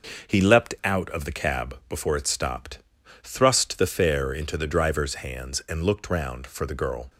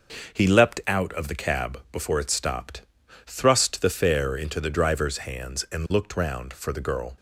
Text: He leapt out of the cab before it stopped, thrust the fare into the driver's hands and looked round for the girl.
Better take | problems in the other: neither | none

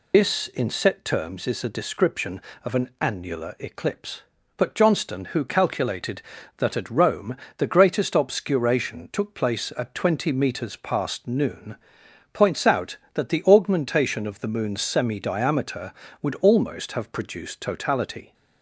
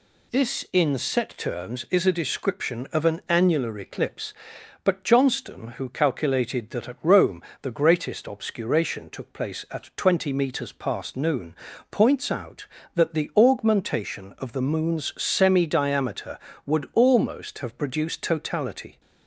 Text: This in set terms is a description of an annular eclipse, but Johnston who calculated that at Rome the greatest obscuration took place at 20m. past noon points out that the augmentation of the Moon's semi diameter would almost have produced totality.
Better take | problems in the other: second | loses the start of "This"; at 0.1 s; 95 ms // pauses between "Rome" and "the"; slight; at 7.3 s; 0.22 s long; slight in the second // pauses between "noon" and "points"; noticeable; at 11.7 s; 0.58 s long; slight in the second

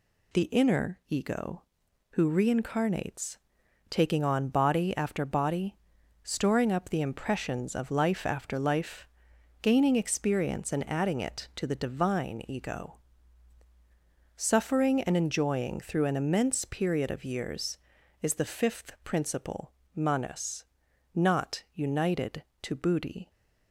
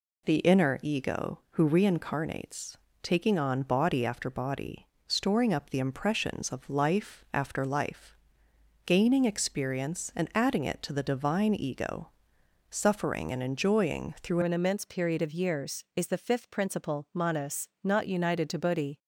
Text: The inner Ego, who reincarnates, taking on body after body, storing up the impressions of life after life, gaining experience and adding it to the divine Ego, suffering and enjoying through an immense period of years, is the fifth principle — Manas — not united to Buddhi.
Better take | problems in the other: first | changes voice at "an"; from 14.4 s on; 4.5 s long

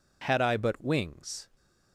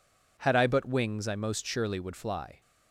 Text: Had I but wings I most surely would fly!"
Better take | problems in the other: second | stops before "I most surely would fly"; at 1.5 s

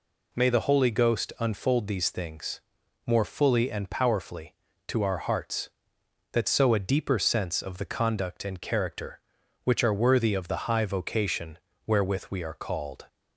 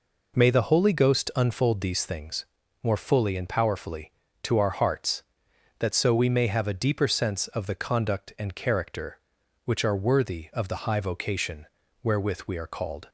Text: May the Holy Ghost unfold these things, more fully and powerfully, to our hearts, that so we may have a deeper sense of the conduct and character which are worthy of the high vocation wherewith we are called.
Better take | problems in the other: second | skips "we may have"; at 6.7 s // pauses between "vocation" and "wherewith"; slight; at 11.5 s; 0.28 s long; slight in the second

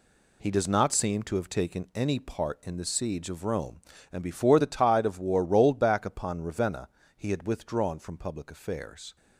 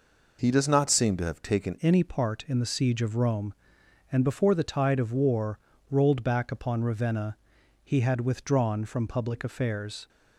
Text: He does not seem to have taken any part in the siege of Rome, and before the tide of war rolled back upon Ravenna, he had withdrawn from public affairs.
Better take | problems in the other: first | changes voice at "any"; from 1.8 s on; 8.2 s long // pauses between "war" and "rolled"; slight; at 5.6 s; 0.28 s long

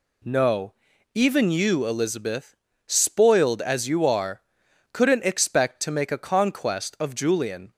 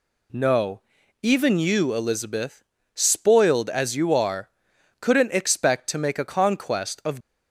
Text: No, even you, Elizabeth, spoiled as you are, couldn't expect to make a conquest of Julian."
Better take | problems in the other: first | stops before "Julian"; at 7.2 s

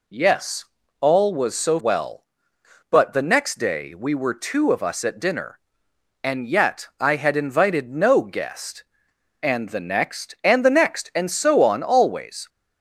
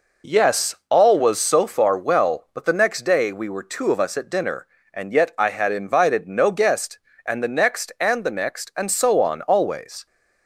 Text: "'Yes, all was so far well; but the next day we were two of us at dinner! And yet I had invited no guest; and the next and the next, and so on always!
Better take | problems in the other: second | skips "far"; at 1.7 s

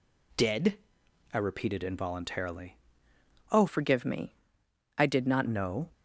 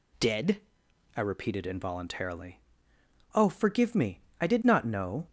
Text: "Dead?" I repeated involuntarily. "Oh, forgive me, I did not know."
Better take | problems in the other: second | changes voice from "forgive" to "not"; from 3.6 to 5.4 s; 1.8 s long

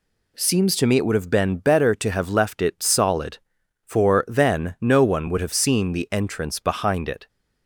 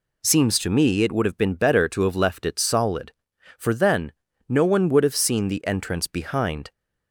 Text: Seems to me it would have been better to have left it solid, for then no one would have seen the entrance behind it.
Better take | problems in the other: first | pauses between "then" and "no"; slight; at 4.1 s; 0.36 s long // stops before "it"; at 6.7 s

